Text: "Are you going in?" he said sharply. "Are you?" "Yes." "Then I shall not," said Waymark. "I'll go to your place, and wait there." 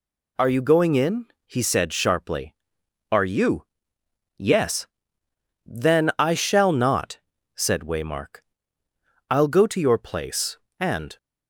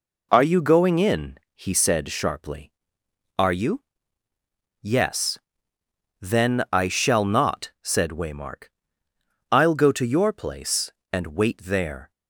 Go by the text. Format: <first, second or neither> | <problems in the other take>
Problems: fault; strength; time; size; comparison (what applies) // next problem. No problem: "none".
second | stops before "wait there"; at 11.1 s